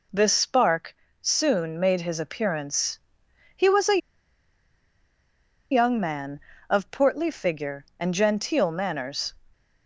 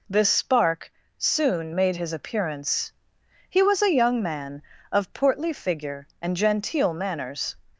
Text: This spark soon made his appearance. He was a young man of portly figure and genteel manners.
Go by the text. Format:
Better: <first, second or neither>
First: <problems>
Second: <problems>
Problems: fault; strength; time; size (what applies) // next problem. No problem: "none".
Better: second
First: pauses between "spark" and "soon"; slight; at 0.9 s; 0.26 s long // pauses between "a" and "young"; strong; at 4.0 s; 1.7 s long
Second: pauses between "spark" and "soon"; slight; at 0.9 s; 0.26 s long